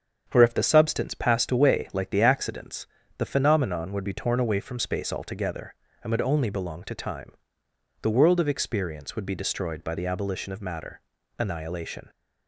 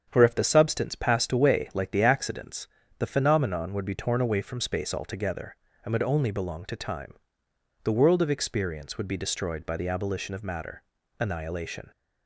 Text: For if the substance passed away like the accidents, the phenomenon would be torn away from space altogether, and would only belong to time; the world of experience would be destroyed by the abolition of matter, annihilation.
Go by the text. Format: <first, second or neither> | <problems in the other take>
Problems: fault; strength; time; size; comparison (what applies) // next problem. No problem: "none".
neither | starts louder than the rest; strong; the same in both